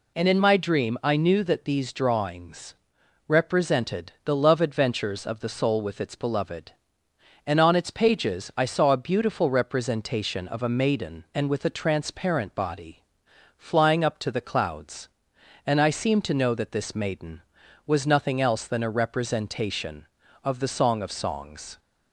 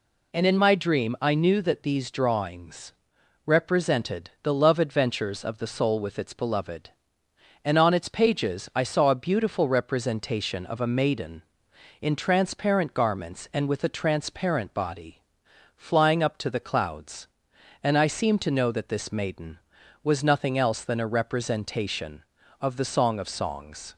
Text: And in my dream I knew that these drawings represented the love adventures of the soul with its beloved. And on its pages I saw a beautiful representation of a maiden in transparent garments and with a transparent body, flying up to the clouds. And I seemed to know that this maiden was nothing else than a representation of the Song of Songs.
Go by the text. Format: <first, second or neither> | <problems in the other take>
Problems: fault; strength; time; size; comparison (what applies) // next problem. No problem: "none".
second | pauses between "drawings" and "represented"; noticeable; at 2.7 s; 0.54 s long; noticeable in the second // skips "in transparent garments"; at 11.2 s